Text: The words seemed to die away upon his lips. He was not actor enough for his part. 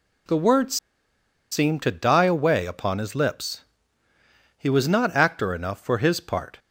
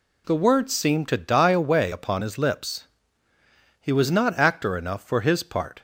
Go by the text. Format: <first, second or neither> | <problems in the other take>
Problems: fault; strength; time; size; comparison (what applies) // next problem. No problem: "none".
second | pauses between "words" and "seemed"; noticeable; at 0.7 s; 0.75 s long